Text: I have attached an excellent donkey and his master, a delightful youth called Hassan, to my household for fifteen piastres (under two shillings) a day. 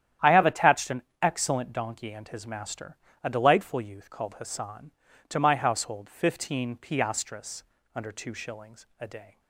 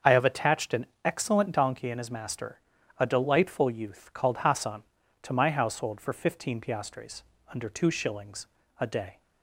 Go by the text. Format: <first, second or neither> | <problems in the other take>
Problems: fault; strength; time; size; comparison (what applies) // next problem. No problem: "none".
second | starts louder than the rest; strong; until 1.4 s; 10.5 dB; also in the second // pauses between "an" and "excellent"; slight; at 1.0 s; 0.20 s long; slight in the second // skips "for"; at 6.0 s